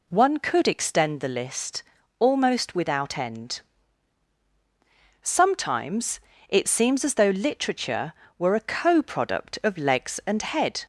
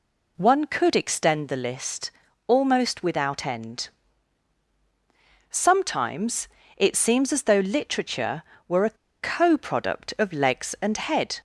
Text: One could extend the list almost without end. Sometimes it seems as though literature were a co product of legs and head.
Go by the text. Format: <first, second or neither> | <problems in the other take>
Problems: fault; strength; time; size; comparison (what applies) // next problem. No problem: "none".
first | pauses between "list" and "almost"; slight; at 2.1 s; 0.36 s long; slight in the first // pauses between "Sometimes" and "it"; slight; at 6.4 s; 0.30 s long; slight in the first // pauses between "a" and "co"; slight; at 8.9 s; 0.25 s long